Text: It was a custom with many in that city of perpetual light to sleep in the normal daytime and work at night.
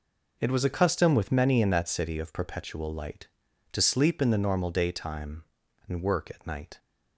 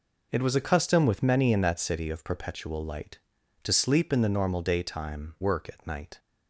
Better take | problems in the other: first | skips "and"; at 5.3 s

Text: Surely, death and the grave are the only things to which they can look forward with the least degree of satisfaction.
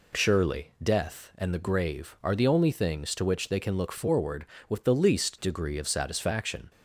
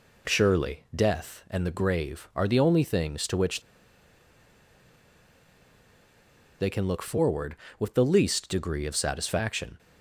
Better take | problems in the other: first | pauses between "which" and "they"; strong; at 3.6 s; 3.0 s long

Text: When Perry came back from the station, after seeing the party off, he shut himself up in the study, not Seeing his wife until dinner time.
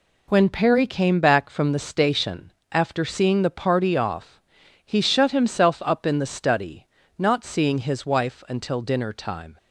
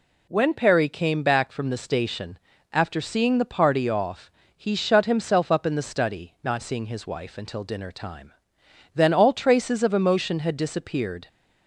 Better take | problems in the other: first | goes on to say "Then all traces of emotion had disappeared"; strong; from 8.9 s on; 2.3 s long

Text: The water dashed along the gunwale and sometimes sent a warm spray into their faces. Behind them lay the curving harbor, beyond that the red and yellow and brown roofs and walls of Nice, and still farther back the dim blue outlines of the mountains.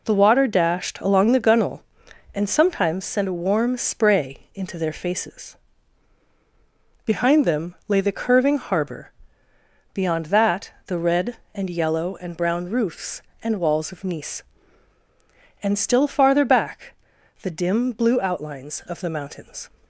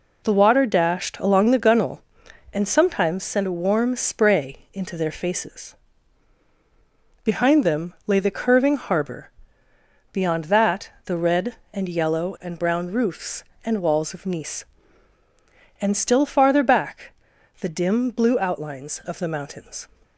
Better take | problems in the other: neither | pauses between "that" and "the"; slight; the same in both // pauses between "back" and "the"; noticeable; the same in both

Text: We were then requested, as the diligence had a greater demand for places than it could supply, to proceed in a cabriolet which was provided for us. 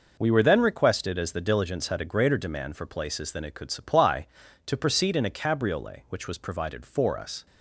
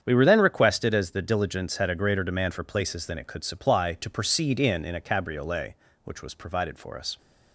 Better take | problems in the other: first | starts louder than the rest; strong; until 1.0 s; 8 dB // says "in" twice; at 4.8 s

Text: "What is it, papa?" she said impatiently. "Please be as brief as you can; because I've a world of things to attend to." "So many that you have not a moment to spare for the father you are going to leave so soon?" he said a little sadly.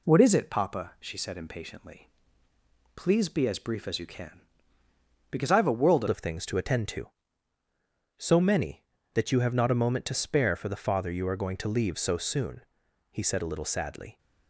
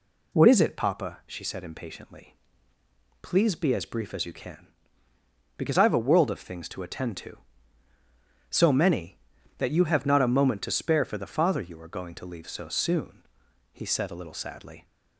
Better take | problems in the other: second | changes voice at "of"; from 6.0 s on; 8.1 s long

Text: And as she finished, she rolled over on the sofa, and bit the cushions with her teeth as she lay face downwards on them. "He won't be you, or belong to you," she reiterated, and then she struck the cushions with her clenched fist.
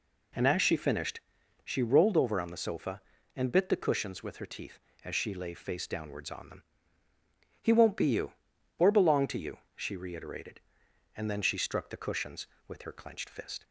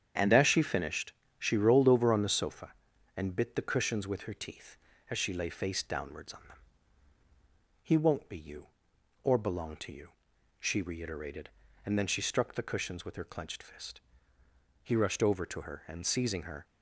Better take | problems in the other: first | starts louder than the rest; strong; until 1.4 s; 8.5 dB // goes on to say "He rushed over to her and seizing her"; strong; from 14.8 s on; 1.8 s long

